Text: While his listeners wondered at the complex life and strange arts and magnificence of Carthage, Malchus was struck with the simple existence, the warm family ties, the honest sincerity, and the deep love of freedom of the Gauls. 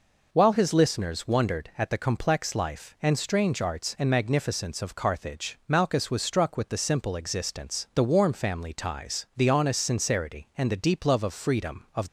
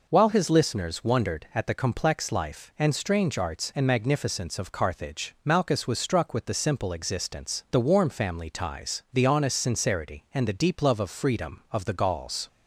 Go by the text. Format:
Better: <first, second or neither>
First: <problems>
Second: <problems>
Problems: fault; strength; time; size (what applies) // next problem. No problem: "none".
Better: second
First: stops before "the Gauls"; at 12.0 s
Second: none